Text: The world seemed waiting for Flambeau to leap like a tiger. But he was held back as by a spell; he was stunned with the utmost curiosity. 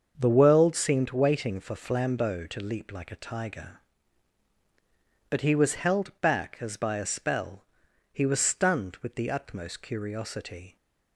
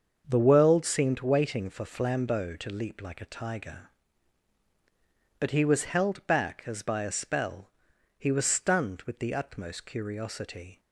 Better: neither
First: starts louder than the rest; until 1.1 s; 6.5 dB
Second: starts louder than the rest; until 1.2 s; 6.5 dB

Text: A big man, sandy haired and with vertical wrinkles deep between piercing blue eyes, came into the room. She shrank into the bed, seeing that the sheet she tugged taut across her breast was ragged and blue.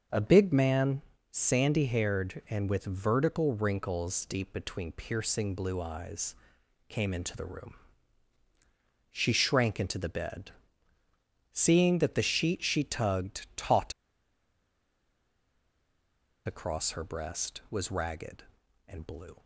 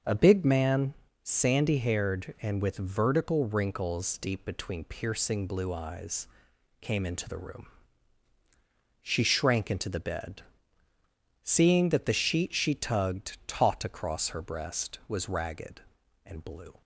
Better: second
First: starts louder than the rest; until 1.3 s; 6 dB // pauses between "taut" and "across"; strong; at 13.9 s; 2.5 s long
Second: starts louder than the rest; until 1.3 s; 6.5 dB

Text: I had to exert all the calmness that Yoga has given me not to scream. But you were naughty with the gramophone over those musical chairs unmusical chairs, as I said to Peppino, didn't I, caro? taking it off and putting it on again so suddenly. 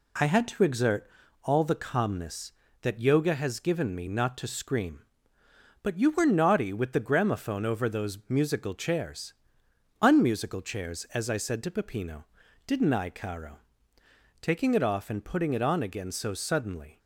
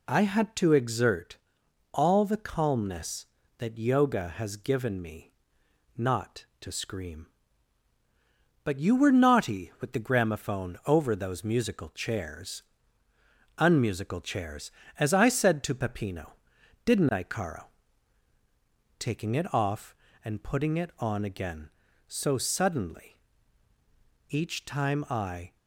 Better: first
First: pauses between "exert" and "all"; slight; at 1.0 s; 0.36 s long // pauses between "chairs" and "unmusical"; noticeable; at 9.3 s; 0.68 s long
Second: pauses between "exert" and "all"; noticeable; at 1.3 s; 0.56 s long // pauses between "me" and "not"; noticeable; at 5.3 s; 0.64 s long // pauses between "chairs" and "unmusical"; noticeable; at 12.6 s; 0.98 s long // goes on to say "Each time I"; noticeable; from 24.2 s on; 1.2 s long

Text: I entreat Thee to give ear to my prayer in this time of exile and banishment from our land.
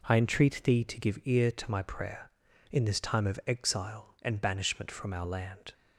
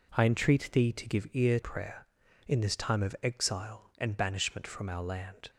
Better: first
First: none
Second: skips "to my"; at 1.6 s

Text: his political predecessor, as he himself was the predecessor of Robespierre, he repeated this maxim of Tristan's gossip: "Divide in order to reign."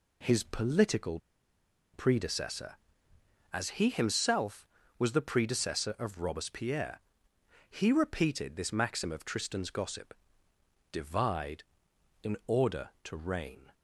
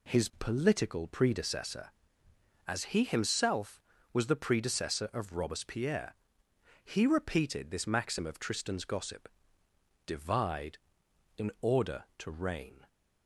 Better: second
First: pauses between "political" and "predecessor"; noticeable; at 1.1 s; 0.76 s long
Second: none

